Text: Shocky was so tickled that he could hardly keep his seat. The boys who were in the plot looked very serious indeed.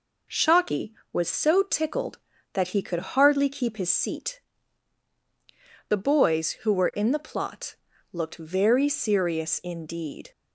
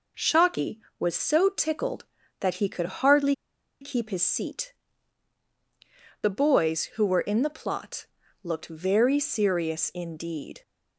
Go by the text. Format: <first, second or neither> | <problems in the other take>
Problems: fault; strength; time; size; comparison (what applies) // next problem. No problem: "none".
first | pauses between "hardly" and "keep"; noticeable; at 3.3 s; 0.46 s long // pauses between "plot" and "looked"; at 8.0 s; 0.38 s long; also in the first